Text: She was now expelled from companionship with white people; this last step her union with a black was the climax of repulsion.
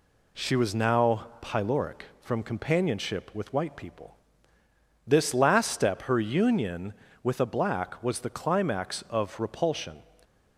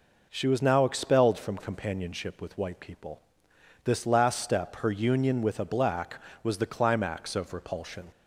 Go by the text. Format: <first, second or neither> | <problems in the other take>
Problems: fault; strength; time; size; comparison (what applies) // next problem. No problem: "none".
second | says "pyloric" for "expelled"; at 1.4 s